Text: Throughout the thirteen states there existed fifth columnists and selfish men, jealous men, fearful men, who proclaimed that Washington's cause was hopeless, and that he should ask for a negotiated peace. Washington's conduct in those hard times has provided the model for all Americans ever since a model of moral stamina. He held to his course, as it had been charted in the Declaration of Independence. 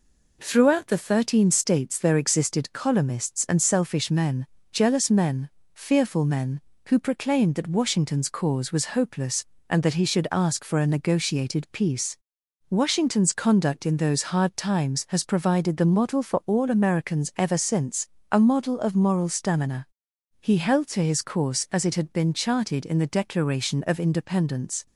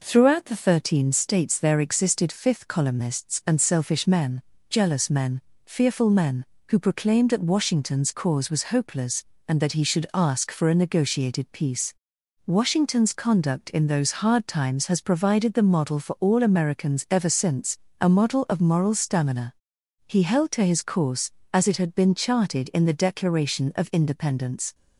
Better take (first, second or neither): second